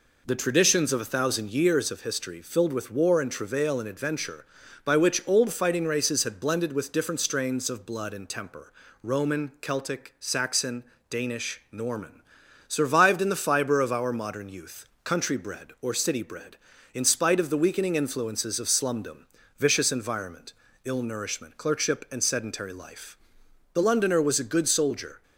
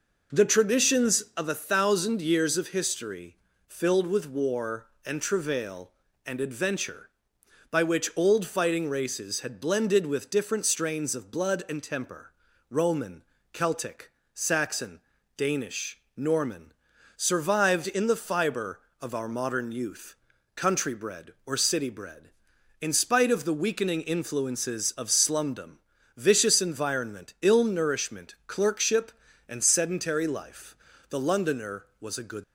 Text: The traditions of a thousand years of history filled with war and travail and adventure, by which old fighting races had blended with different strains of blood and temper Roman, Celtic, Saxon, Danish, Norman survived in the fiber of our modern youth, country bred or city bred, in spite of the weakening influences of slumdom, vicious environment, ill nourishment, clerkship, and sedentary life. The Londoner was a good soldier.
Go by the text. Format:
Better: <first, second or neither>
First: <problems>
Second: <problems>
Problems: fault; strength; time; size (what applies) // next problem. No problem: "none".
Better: first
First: pauses between "temper" and "Roman"; slight; at 8.7 s; 0.32 s long // pauses between "Norman" and "survived"; at 12.2 s; 0.44 s long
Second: pauses between "history" and "filled"; slight; at 3.3 s; 0.32 s long // pauses between "temper" and "Roman"; at 12.3 s; 0.38 s long // pauses between "Norman" and "survived"; at 16.7 s; 0.44 s long // stops before "soldier"; at 32.4 s